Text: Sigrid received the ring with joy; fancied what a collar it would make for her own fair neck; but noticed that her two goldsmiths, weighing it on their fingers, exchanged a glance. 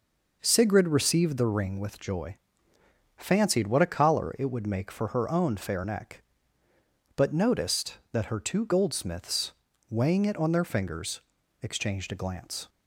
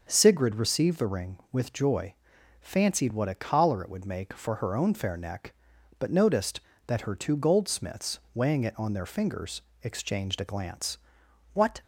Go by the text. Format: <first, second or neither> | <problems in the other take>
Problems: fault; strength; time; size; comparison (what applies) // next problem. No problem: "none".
first | starts louder than the rest; until 1.1 s; 6.5 dB // goes on to say "What"; slight; from 11.5 s on; 0.28 s long